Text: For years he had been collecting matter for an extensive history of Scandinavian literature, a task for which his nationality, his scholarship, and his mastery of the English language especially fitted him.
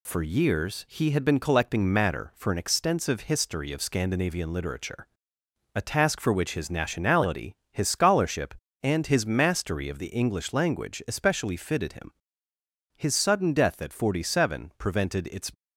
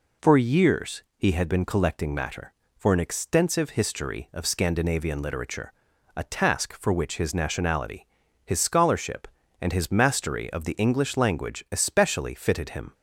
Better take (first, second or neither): second